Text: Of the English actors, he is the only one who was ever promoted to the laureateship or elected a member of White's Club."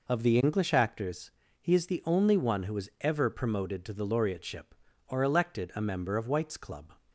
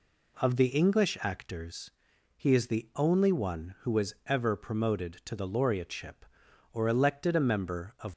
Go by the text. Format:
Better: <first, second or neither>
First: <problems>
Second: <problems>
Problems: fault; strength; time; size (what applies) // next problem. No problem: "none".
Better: first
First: none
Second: stops before "White's Club"; at 8.1 s